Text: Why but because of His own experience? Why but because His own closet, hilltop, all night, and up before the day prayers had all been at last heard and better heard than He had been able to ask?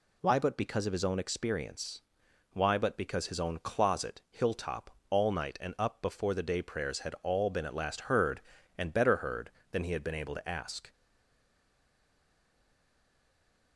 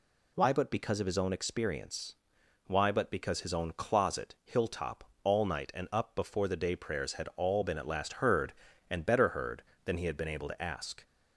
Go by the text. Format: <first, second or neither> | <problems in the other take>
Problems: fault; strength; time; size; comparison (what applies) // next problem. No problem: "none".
second | stays silent after the last word; strong; from 10.9 s on; 2.8 s long